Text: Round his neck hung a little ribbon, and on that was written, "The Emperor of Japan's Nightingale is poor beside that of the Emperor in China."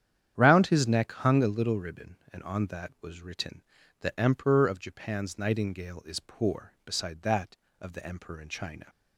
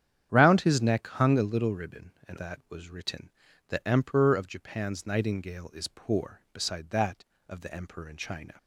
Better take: first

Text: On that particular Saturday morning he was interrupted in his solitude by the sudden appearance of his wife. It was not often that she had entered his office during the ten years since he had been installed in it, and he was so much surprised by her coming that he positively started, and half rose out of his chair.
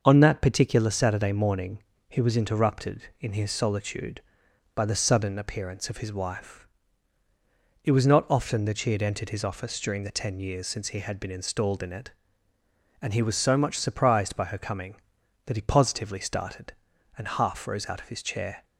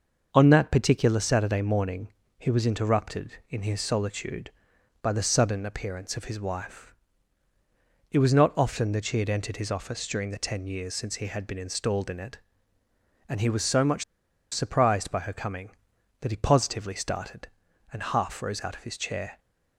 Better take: first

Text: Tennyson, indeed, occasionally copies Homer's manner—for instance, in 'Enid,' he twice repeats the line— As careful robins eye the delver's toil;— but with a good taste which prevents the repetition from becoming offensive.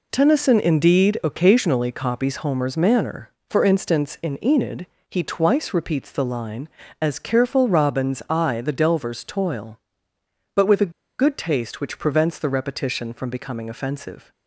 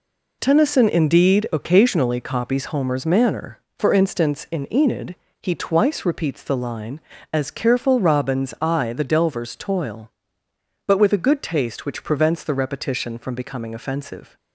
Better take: second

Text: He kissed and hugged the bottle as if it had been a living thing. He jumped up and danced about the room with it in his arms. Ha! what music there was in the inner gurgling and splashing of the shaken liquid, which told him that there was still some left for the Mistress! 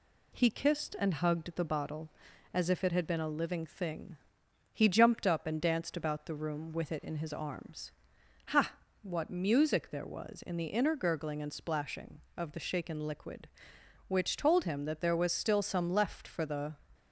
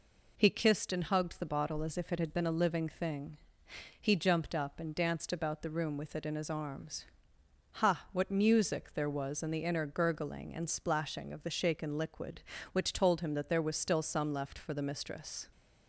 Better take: second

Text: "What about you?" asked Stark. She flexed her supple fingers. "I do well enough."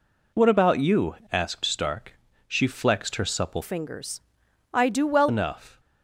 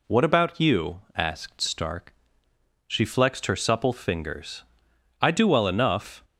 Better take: second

